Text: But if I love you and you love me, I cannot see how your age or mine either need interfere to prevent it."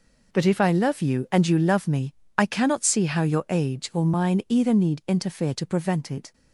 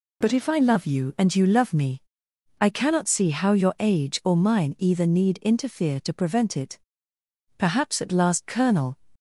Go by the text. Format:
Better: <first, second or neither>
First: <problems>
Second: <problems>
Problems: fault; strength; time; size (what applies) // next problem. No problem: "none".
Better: first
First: none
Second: goes on to say "Perhaps at last Colonel"; from 7.5 s on; 1.4 s long